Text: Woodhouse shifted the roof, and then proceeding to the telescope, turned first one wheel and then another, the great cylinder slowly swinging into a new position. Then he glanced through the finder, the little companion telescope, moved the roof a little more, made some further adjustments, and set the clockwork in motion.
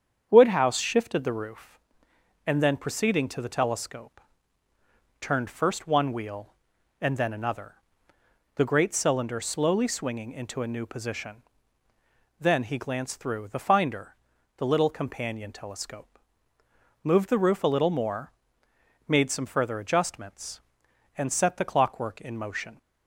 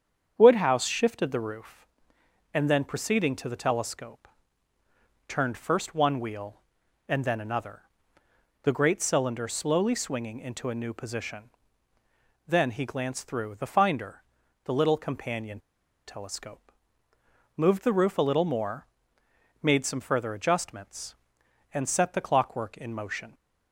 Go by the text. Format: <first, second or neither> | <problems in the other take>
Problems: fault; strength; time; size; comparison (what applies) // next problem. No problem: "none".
first | starts louder than the rest; strong; until 1.3 s; 7.5 dB; strong in the first // pauses between "companion" and "telescope"; noticeable; at 15.5 s; 0.48 s long